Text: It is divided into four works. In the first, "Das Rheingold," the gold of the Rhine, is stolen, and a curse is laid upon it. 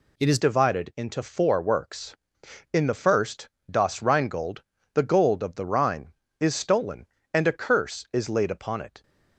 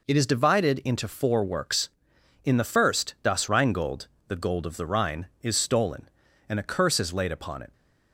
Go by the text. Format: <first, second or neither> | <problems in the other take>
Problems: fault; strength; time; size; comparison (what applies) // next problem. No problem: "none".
second | changes voice at "divided"; from 0.3 s on; 8.7 s long